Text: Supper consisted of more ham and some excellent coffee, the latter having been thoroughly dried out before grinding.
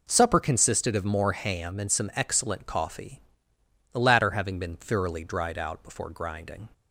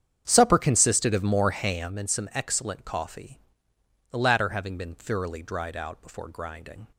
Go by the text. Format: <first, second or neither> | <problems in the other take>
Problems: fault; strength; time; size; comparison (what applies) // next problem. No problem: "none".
first | starts louder than the rest; strong; until 2.0 s; 8.5 dB